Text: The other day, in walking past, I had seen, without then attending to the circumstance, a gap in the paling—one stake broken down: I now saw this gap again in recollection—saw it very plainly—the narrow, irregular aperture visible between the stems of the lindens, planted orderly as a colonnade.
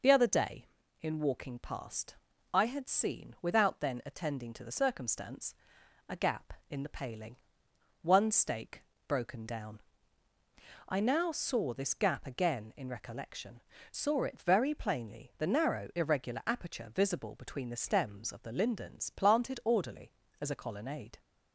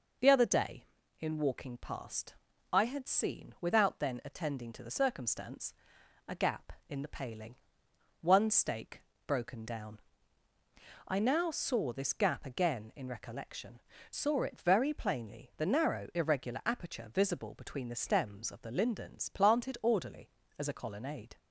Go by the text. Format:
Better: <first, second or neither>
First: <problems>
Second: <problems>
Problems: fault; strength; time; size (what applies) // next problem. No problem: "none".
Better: neither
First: pauses between "stake" and "broken"; slight; at 8.8 s; 0.26 s long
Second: pauses between "stake" and "broken"; slight; at 9.0 s; 0.26 s long